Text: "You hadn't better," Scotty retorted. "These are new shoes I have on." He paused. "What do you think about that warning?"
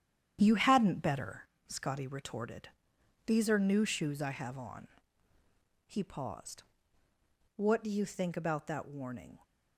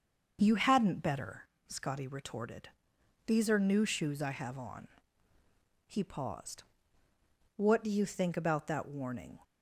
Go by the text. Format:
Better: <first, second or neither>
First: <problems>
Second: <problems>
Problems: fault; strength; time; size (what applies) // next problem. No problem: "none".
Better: second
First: gets quieter; strong; throughout; 7.5 dB // starts louder than the rest; strong; until 1.4 s; 9.5 dB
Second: starts louder than the rest; until 1.4 s; 6.5 dB